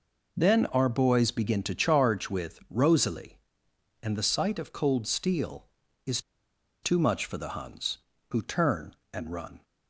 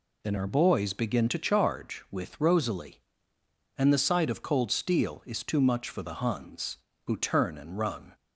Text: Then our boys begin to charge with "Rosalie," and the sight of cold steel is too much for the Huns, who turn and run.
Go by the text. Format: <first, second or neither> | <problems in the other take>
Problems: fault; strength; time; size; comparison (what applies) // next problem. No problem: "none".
second | pauses between "is" and "too"; noticeable; at 6.1 s; 0.63 s long